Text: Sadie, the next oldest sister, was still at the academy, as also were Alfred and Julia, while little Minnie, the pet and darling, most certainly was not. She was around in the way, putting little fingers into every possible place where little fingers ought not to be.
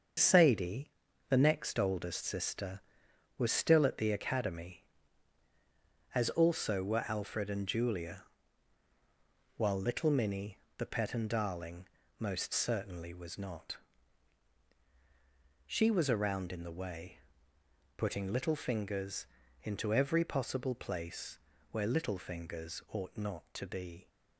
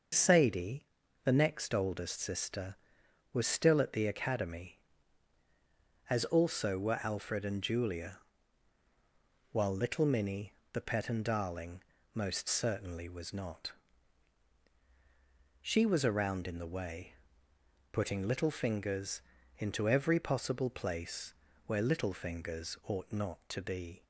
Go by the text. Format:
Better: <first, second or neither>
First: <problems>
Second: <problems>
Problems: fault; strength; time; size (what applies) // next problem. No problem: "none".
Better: second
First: gets quieter; throughout; 6 dB // starts louder than the rest; until 1.5 s; 7 dB // pauses between "fingers" and "into"; slight; at 19.2 s; 0.36 s long // pauses between "place" and "where"; slight; at 21.3 s; 0.32 s long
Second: starts louder than the rest; until 1.5 s; 6.5 dB // pauses between "fingers" and "into"; slight; at 19.2 s; 0.36 s long // pauses between "place" and "where"; slight; at 21.3 s; 0.32 s long